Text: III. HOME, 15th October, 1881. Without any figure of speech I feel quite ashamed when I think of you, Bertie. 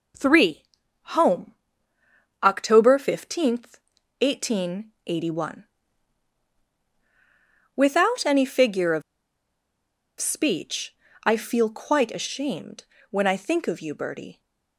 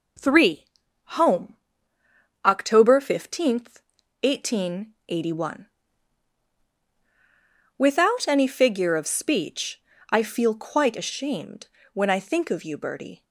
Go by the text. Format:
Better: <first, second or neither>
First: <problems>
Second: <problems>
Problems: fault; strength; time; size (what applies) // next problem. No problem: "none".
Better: second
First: pauses between "of" and "speech"; at 9.0 s; 1.1 s long // pauses between "speech" and "I"; slight; at 10.9 s; 0.30 s long // pauses between "ashamed" and "when"; slight; at 12.8 s; 0.28 s long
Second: pauses between "speech" and "I"; slight; at 9.7 s; 0.30 s long // pauses between "ashamed" and "when"; slight; at 11.6 s; 0.28 s long